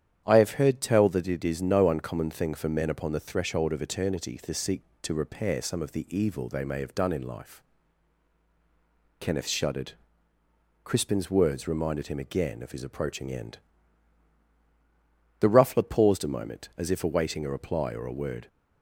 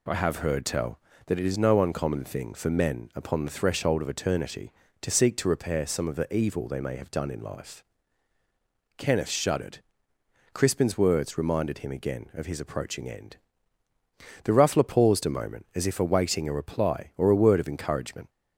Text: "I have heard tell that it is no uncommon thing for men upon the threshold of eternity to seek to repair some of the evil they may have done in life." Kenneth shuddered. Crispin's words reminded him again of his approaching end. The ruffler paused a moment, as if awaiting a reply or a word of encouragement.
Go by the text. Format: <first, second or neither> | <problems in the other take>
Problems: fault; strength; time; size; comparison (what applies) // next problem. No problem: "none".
second | starts louder than the rest; strong; until 1.2 s; 9.5 dB // stops before "of encouragement"; at 18.4 s